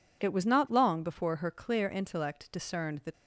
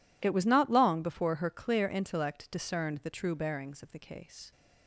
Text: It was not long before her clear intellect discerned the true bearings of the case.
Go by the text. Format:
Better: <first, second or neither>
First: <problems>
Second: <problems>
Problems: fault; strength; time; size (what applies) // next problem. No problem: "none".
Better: second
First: stops before "true bearings of the case"; at 3.1 s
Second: none